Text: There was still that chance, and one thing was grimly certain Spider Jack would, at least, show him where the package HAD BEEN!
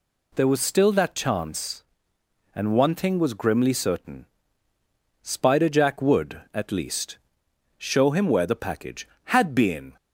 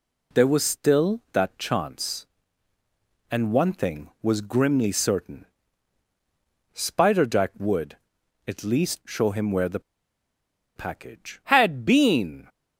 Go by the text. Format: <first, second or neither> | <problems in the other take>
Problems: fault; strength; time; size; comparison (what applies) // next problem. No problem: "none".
first | pauses between "certain" and "Spider"; strong; at 5.4 s; 1.2 s long; noticeable in the first // pauses between "the" and "package"; noticeable; at 9.7 s; 0.95 s long